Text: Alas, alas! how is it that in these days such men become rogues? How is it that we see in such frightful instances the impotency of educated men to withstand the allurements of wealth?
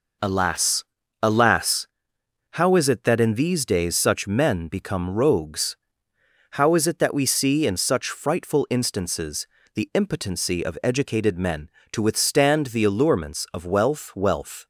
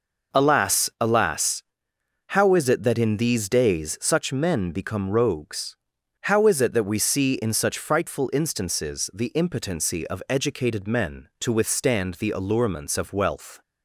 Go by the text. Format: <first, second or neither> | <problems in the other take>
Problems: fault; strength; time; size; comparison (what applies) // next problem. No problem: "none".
second | pauses between "instances" and "the"; slight; at 9.4 s; 0.28 s long // says "wealth" twice; at 14.1 s